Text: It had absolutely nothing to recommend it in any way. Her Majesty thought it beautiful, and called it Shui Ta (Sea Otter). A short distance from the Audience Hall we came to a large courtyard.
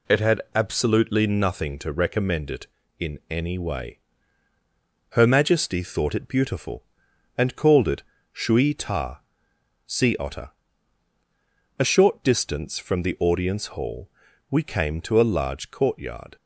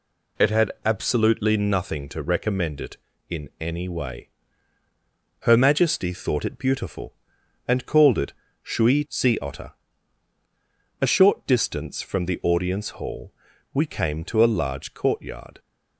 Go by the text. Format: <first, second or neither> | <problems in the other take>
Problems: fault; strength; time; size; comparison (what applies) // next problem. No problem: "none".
first | pauses between "it" and "Shui"; slight; at 8.3 s; 0.28 s long; slight in the first // skips "Ta"; at 9.0 s // pauses between "Hall" and "we"; at 13.3 s; 0.40 s long; also in the first